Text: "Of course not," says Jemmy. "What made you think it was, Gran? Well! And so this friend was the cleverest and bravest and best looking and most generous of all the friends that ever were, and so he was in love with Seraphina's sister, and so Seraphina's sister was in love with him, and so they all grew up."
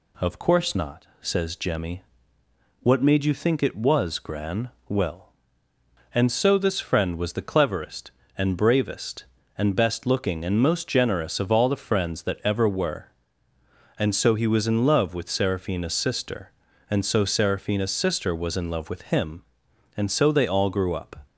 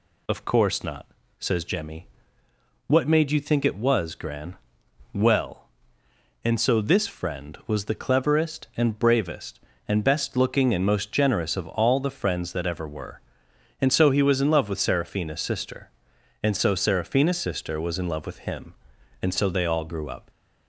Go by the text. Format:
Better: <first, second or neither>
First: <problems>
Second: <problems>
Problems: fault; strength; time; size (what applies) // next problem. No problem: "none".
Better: neither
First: none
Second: none